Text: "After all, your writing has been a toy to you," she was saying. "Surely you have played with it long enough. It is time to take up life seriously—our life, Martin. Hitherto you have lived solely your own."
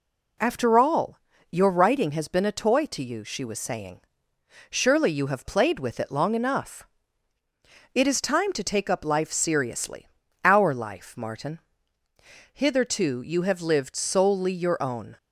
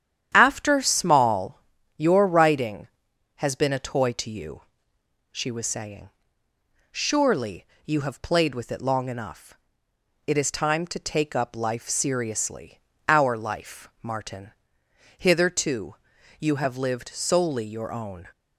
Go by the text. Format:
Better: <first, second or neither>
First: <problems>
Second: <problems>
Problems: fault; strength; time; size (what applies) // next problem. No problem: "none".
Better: first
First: none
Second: starts louder than the rest; strong; until 1.3 s; 10 dB // says "small" for "all"; at 0.8 s // pauses between "Surely" and "you"; slight; at 7.6 s; 0.18 s long // pauses between "Hitherto" and "you"; at 15.9 s; 0.42 s long